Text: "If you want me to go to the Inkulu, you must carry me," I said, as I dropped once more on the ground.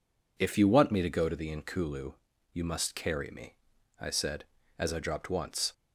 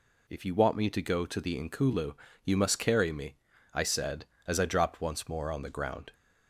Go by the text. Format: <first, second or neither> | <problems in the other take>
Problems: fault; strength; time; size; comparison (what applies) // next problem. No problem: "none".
second | stops before "more on the ground"; at 5.7 s